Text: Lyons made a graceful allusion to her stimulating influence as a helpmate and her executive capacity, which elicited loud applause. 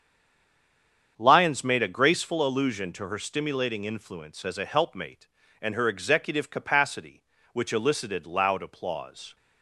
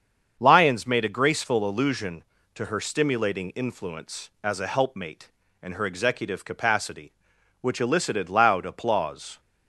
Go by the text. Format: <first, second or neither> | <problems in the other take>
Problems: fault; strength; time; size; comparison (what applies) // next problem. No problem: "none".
second | stays silent before the first word; noticeable; until 1.1 s; 1.1 s long // starts louder than the rest; strong; until 2.1 s; 7.5 dB; also in the second